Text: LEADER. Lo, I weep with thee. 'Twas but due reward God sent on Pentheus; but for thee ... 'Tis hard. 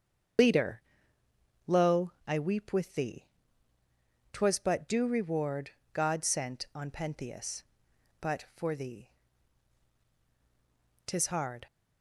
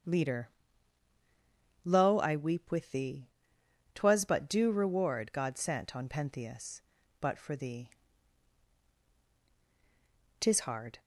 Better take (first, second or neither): second